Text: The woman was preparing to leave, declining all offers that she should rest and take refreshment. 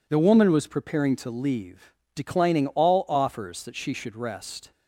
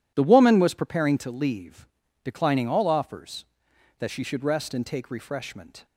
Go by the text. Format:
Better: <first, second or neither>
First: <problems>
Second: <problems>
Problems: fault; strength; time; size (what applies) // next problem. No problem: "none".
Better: second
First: stops before "and take refreshment"; at 4.7 s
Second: none